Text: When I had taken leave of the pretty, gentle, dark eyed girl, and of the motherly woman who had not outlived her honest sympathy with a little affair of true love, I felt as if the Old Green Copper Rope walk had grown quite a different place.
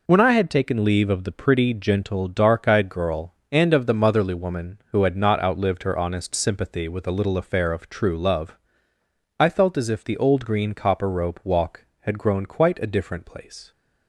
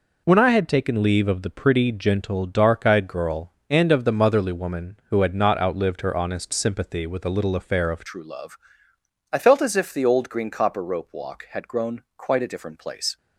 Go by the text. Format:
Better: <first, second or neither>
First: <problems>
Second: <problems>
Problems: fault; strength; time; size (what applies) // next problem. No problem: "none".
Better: first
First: none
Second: changes voice at "true"; from 8.0 s on; 5.1 s long